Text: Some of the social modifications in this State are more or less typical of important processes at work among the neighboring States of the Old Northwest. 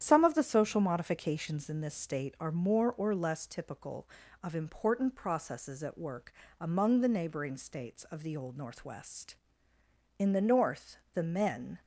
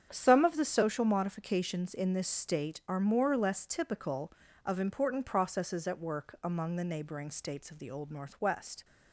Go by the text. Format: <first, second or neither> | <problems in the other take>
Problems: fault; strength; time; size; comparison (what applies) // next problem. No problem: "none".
second | starts louder than the rest; strong; until 1.0 s; 10 dB; strong in the second // pauses between "work" and "among"; slight; at 6.3 s; 0.26 s long // goes on to say "In the north the men"; from 10.1 s on; 1.6 s long